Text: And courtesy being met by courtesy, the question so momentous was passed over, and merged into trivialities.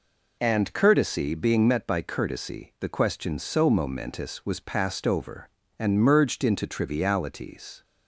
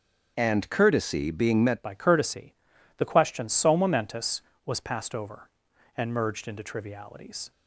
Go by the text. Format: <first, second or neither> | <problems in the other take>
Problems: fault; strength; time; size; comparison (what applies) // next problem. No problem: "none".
first | starts louder than the rest; until 1.3 s; 6.5 dB // changes voice at "by"; from 1.8 s on; 5.7 s long